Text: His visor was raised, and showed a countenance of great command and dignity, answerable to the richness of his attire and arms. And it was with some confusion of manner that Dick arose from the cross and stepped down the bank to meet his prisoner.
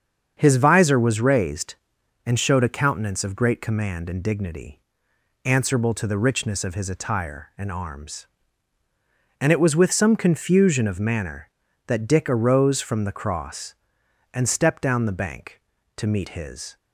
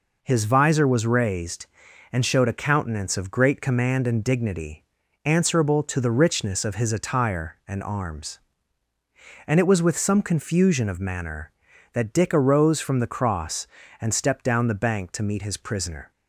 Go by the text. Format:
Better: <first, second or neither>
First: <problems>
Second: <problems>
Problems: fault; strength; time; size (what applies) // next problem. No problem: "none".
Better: second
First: starts louder than the rest; strong; until 1.3 s; 7 dB // stops before "prisoner"; at 16.7 s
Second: none